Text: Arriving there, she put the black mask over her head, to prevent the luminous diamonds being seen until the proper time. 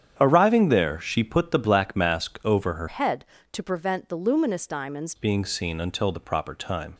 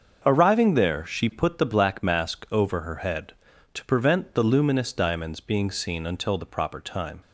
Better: second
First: starts louder than the rest; strong; until 1.2 s; 9 dB // changes voice from "head" to "diamonds"; from 2.8 to 5.1 s; 2.3 s long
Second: starts louder than the rest; until 1.2 s; 6.5 dB

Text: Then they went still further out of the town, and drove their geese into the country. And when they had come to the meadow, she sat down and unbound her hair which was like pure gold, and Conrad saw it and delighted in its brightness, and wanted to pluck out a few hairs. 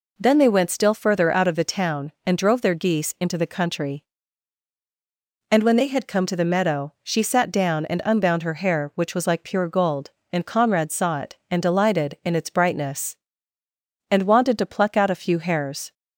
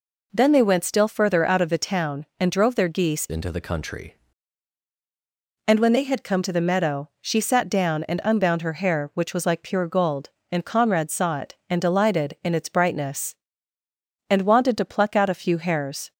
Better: first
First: none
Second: changes voice from "into" to "country"; from 3.2 to 4.1 s; 0.9 s long

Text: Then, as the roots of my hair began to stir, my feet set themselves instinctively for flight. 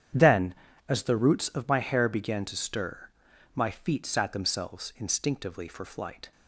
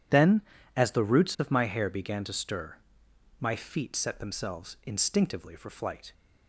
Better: second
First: starts louder than the rest; strong; until 1.5 s; 9 dB // says "sat" for "set"; at 4.0 s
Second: none

